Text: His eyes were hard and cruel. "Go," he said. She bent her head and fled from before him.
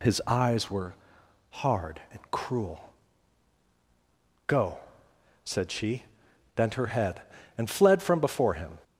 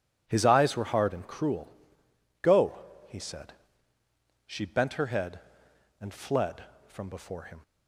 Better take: second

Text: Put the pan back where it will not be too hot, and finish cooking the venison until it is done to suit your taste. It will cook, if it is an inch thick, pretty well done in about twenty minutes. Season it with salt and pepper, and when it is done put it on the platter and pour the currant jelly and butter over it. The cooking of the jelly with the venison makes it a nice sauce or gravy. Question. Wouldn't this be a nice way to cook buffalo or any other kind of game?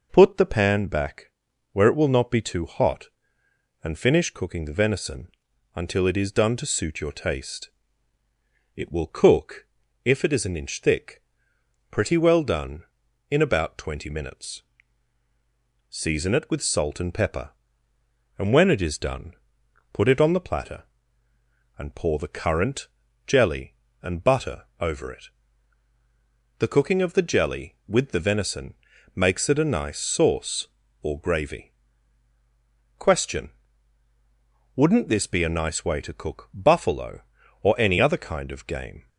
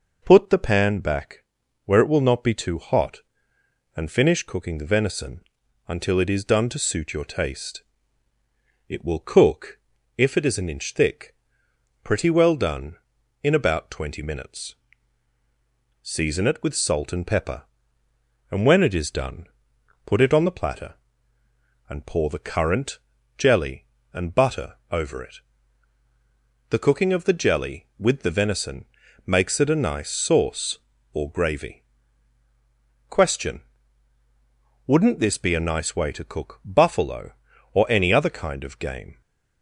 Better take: neither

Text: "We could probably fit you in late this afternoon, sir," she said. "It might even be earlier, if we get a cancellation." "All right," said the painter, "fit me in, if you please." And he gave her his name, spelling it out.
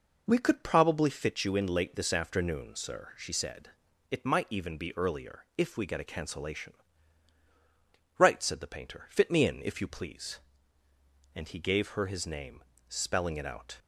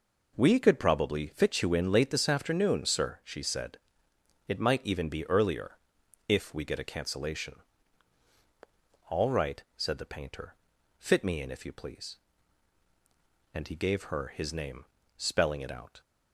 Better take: second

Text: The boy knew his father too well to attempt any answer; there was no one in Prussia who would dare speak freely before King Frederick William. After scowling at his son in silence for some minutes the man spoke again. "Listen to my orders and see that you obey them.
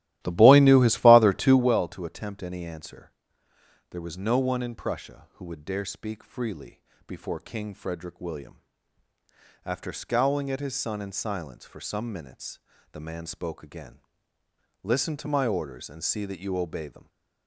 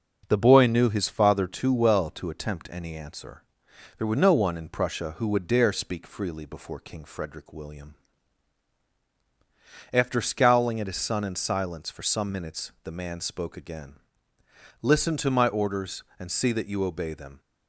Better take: second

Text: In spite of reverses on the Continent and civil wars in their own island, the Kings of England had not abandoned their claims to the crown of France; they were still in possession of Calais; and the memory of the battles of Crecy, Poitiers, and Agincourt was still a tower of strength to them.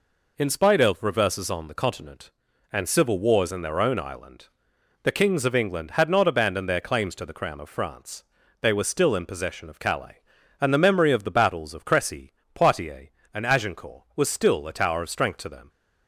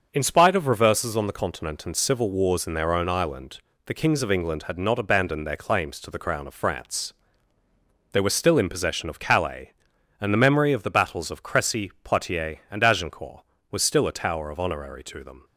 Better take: first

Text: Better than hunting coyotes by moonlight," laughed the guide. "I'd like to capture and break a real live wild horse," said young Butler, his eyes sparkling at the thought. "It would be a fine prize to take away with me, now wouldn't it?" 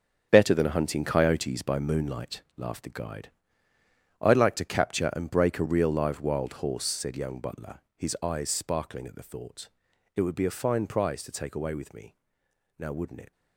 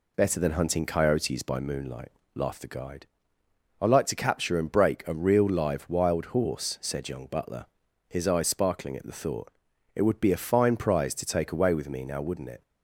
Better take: second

